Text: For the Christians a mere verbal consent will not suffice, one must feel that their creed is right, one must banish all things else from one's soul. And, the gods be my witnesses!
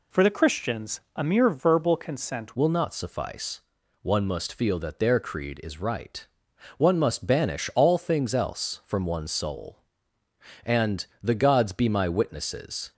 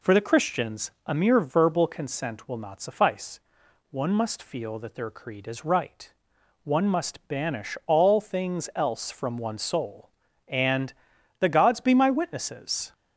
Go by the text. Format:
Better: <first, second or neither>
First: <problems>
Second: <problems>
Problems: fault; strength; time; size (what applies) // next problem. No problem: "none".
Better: second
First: pauses between "Christians" and "a"; slight; at 0.9 s; 0.16 s long // changes voice at "will"; from 2.5 s on; 10.4 s long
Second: pauses between "Christians" and "a"; slight; at 0.9 s; 0.16 s long